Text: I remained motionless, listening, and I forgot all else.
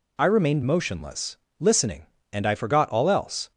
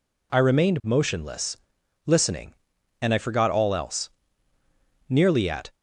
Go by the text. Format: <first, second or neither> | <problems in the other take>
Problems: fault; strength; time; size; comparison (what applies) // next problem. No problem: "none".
first | goes on to say "Nearly at"; noticeable; from 5.0 s on; 0.66 s long